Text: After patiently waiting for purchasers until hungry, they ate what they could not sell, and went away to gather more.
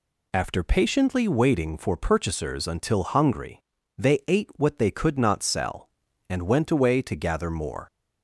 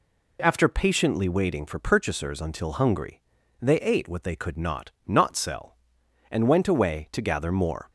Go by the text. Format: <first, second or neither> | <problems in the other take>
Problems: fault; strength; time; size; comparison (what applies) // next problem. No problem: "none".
first | says "not" twice; at 5.0 s